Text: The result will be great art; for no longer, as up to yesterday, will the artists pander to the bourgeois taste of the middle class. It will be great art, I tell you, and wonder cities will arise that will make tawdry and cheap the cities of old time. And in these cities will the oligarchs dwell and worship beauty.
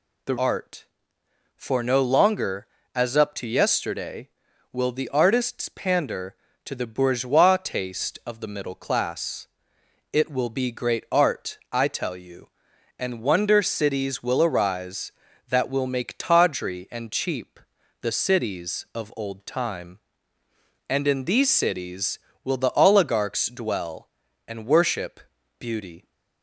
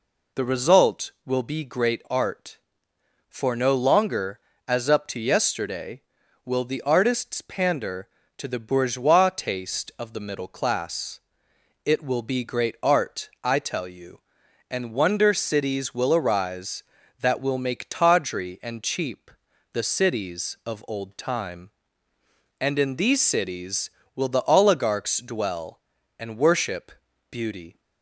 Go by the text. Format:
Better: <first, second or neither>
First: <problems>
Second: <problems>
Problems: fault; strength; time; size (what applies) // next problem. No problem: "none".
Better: second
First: skips "result will be great"; at 0.3 s // pauses between "cheap" and "the"; at 17.5 s; 0.44 s long // pauses between "worship" and "beauty"; at 25.1 s; 0.40 s long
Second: pauses between "cheap" and "the"; at 19.2 s; 0.44 s long // pauses between "worship" and "beauty"; at 26.8 s; 0.40 s long